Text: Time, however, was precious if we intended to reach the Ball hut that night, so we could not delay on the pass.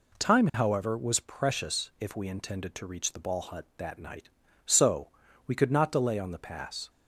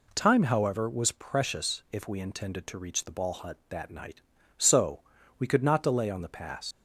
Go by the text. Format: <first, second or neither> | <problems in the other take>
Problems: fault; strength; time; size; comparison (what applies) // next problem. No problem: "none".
first | pauses between "so" and "we"; slight; at 5.0 s; 0.36 s long; slight in the first // leaves "pass" unfinished; at 6.7 s; 85 ms